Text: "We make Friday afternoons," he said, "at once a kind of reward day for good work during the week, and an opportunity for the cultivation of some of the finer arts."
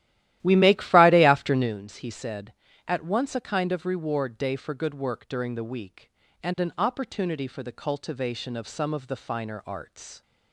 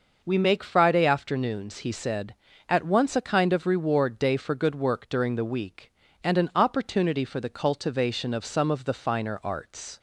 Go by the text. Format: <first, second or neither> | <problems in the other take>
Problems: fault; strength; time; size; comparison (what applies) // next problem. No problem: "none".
second | starts louder than the rest; strong; until 1.8 s; 14 dB